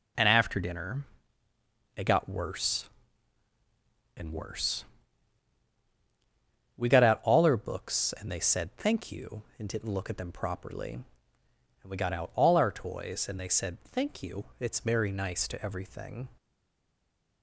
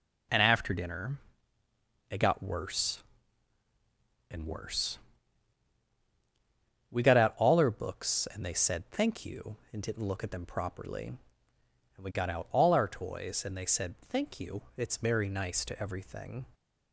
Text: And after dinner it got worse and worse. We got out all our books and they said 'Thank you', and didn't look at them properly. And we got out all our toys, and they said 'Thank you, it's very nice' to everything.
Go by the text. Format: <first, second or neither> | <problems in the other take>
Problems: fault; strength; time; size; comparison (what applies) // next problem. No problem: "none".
second | pauses between "dinner" and "it"; noticeable; at 1.0 s; 0.92 s long; noticeable in the second // stays silent after the last word; from 16.3 s on; 1.1 s long